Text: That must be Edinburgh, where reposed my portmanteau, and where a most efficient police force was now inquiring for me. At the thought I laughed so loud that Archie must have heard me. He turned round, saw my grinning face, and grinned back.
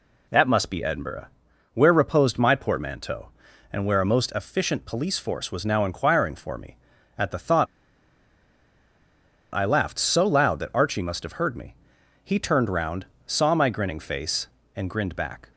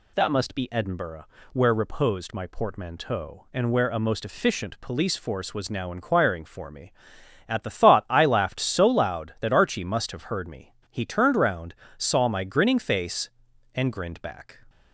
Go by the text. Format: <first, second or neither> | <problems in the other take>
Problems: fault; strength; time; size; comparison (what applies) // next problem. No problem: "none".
second | pauses between "thought" and "I"; strong; at 7.6 s; 1.8 s long